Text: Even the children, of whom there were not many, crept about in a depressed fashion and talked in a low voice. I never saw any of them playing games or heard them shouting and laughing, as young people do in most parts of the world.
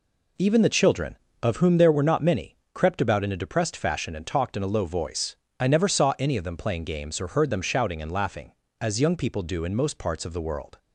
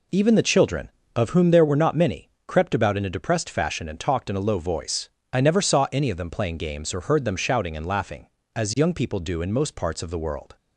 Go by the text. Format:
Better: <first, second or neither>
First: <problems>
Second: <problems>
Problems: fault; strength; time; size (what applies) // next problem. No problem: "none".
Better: neither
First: none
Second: none